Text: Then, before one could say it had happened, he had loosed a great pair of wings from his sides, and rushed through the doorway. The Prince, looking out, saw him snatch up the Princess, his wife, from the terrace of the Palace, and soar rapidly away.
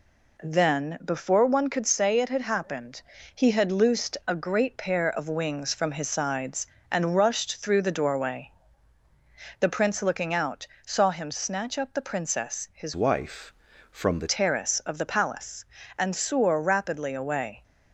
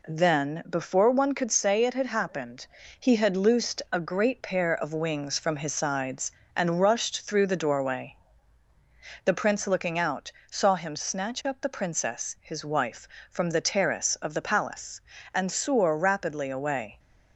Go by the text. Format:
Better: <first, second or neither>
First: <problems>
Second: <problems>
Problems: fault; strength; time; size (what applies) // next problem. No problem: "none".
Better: second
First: changes voice from "wife" to "the"; from 12.9 to 14.2 s; 1.3 s long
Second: none